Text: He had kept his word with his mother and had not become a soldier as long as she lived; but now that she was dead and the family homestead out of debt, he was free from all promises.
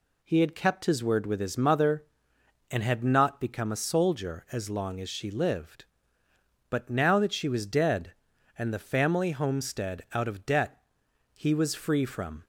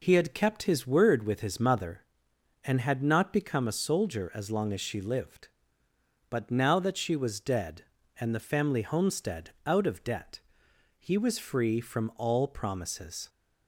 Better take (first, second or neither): second